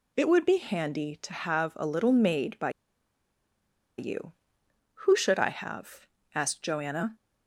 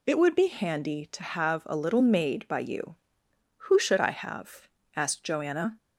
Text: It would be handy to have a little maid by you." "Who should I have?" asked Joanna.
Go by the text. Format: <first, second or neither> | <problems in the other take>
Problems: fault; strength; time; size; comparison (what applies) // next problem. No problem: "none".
second | pauses between "by" and "you"; strong; at 2.6 s; 1.2 s long